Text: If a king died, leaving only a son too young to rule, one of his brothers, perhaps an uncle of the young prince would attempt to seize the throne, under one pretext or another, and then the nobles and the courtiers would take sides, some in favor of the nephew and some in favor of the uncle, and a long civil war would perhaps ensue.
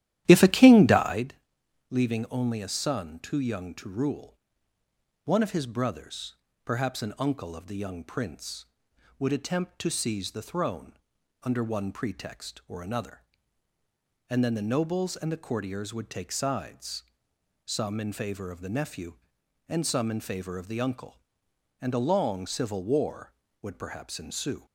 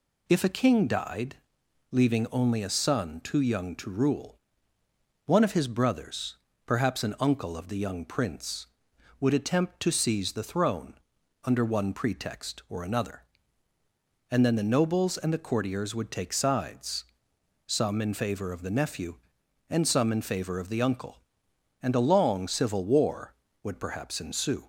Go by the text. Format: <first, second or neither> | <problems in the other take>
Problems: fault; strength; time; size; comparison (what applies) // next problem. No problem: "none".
second | starts louder than the rest; strong; until 1.3 s; 13 dB